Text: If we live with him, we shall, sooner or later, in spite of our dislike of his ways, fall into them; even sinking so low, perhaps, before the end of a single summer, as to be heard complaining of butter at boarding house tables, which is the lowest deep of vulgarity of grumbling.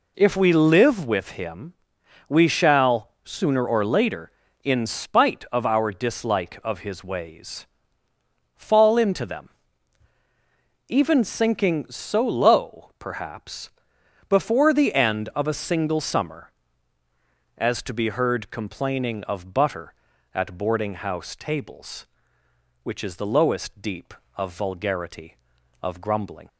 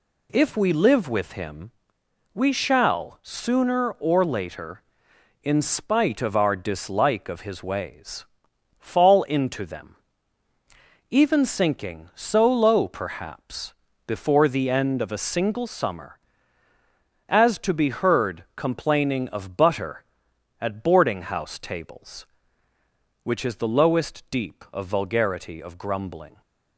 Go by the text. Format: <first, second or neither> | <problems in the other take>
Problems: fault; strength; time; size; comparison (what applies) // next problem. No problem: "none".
neither | none